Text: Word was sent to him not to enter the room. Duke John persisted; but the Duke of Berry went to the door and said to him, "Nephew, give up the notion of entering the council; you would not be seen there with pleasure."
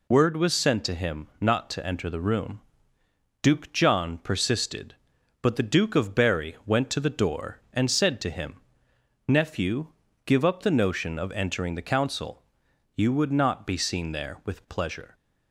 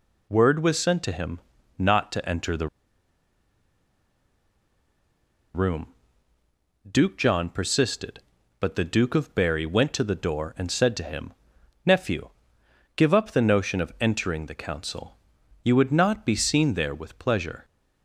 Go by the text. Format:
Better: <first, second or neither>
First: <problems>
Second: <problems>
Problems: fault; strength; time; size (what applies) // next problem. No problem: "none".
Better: first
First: none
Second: pauses between "him" and "not"; at 1.3 s; 0.38 s long // pauses between "the" and "room"; strong; at 2.6 s; 2.8 s long